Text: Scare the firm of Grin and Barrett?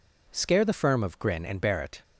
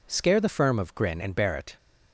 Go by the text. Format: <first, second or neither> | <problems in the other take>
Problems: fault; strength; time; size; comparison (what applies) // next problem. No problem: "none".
neither | none